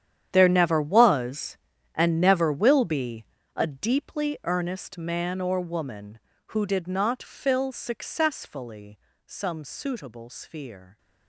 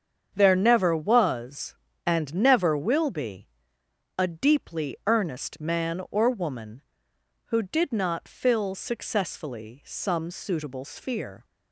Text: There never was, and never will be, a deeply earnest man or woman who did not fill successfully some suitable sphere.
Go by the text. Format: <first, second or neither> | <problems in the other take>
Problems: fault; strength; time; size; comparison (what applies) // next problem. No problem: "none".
second | gets quieter; strong; throughout; 17 dB // starts louder than the rest; strong; until 1.3 s; 9.5 dB; strong in the second // pauses between "successfully" and "some"; slight; at 8.9 s; 0.28 s long